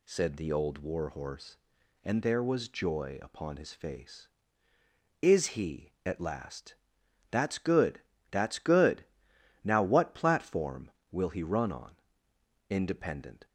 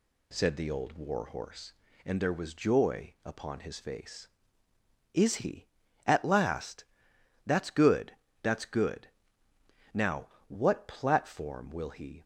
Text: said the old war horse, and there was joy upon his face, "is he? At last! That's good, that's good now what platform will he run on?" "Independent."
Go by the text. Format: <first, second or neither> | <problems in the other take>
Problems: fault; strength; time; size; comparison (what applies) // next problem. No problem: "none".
first | pauses between "good" and "now"; noticeable; at 9.0 s; 0.84 s long; noticeable in the first // pauses between "now" and "what"; slight; at 10.2 s; 0.22 s long // stops before "run on Independent"; at 12.2 s